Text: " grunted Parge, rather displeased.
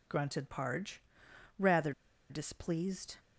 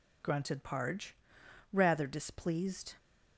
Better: second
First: pauses between "rather" and "displeased"; at 1.9 s; 0.38 s long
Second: none

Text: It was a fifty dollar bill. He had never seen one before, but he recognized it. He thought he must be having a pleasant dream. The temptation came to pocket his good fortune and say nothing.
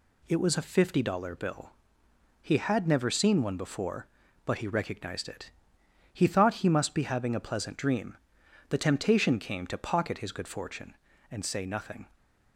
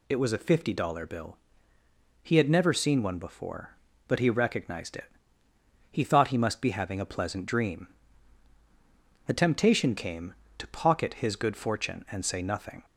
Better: neither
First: none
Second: none

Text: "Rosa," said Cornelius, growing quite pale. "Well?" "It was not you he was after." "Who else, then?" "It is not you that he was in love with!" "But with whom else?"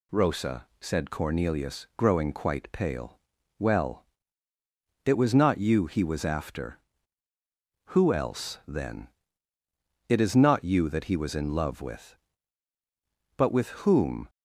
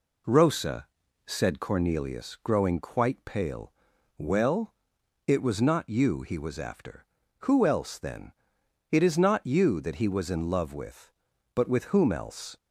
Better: second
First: pauses between "with" and "whom"; slight; at 13.6 s; 0.16 s long // stops before "else"; at 14.2 s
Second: none

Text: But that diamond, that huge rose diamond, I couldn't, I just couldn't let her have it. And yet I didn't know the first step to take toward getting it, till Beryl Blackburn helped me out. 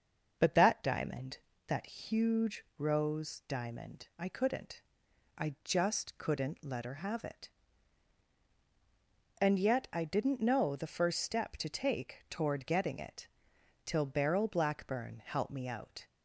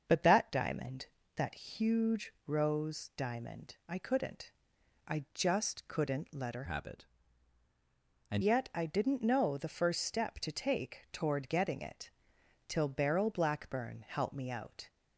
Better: first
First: starts louder than the rest; until 1.7 s; 6.5 dB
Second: starts louder than the rest; until 1.3 s; 7 dB // changes voice from "have" to "And"; from 6.6 to 8.4 s; 1.8 s long

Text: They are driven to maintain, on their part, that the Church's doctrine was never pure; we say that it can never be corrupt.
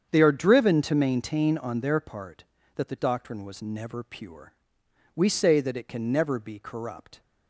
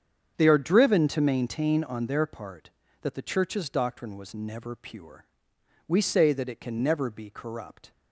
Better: second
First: starts louder than the rest; strong; until 1.1 s; 7.5 dB // skips "Church's"; at 2.9 s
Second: starts louder than the rest; strong; until 1.4 s; 7.5 dB

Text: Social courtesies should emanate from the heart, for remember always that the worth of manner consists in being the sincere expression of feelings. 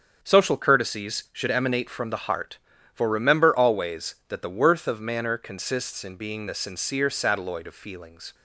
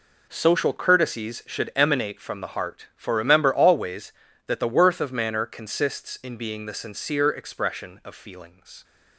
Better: second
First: starts louder than the rest; strong; until 1.2 s; 7 dB // says "satelloid" for "expression"; at 7.0 s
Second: none

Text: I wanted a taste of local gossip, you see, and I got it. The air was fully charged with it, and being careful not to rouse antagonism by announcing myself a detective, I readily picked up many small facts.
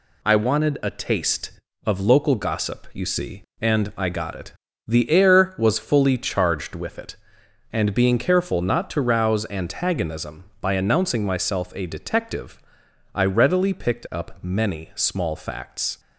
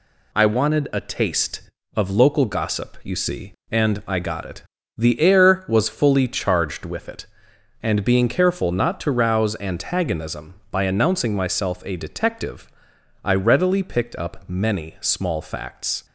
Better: neither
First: none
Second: none

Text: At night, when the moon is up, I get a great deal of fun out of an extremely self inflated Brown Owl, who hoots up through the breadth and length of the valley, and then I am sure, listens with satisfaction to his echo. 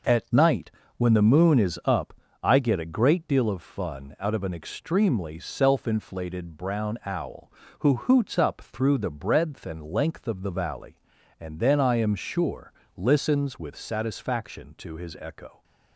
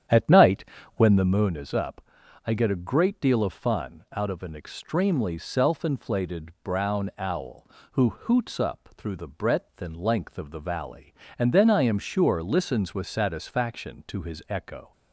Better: first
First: none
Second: starts louder than the rest; strong; until 1.5 s; 9.5 dB

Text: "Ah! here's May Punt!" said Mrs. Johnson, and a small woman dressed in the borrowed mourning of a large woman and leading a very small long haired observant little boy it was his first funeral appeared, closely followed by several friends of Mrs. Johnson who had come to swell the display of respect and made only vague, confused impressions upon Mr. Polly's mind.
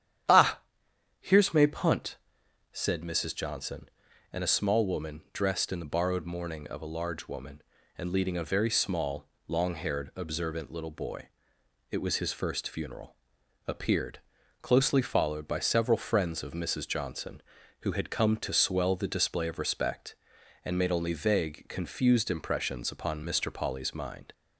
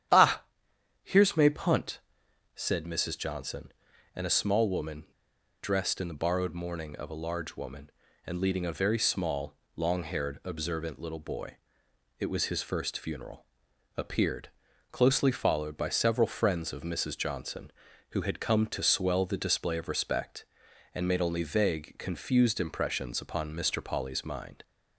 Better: first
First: starts louder than the rest; strong; until 1.8 s; 10 dB // pauses between "small" and "long"; slight; at 9.2 s; 0.22 s long // pauses between "boy" and "it"; noticeable; at 11.2 s; 0.62 s long // pauses between "funeral" and "appeared"; noticeable; at 13.1 s; 0.52 s long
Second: starts louder than the rest; strong; until 1.6 s; 10 dB // pauses between "woman" and "dressed"; noticeable; at 5.0 s; 0.59 s long // pauses between "small" and "long"; slight; at 9.5 s; 0.22 s long // pauses between "boy" and "it"; noticeable; at 11.5 s; 0.62 s long // pauses between "funeral" and "appeared"; noticeable; at 13.4 s; 0.52 s long

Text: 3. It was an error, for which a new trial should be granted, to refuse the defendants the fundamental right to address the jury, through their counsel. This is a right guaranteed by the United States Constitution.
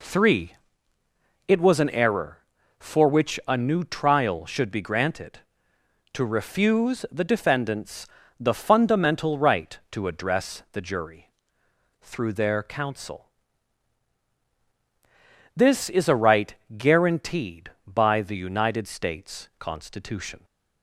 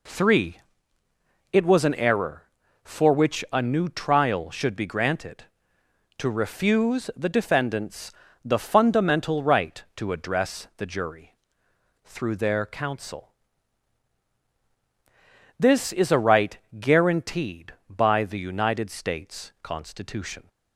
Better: neither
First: pauses between "defendants" and "the"; slight; at 8.0 s; 0.30 s long // pauses between "right" and "guaranteed"; slight; at 16.5 s; 0.20 s long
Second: pauses between "defendants" and "the"; slight; at 8.1 s; 0.30 s long // pauses between "right" and "guaranteed"; slight; at 16.5 s; 0.19 s long

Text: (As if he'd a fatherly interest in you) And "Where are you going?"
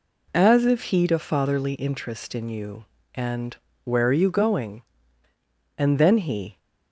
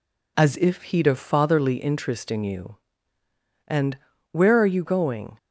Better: second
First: pauses between "And" and "Where"; slight; at 3.5 s; 0.30 s long // goes on to say "And then he"; noticeable; from 5.7 s on; 0.80 s long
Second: pauses between "And" and "Where"; slight; at 3.9 s; 0.35 s long

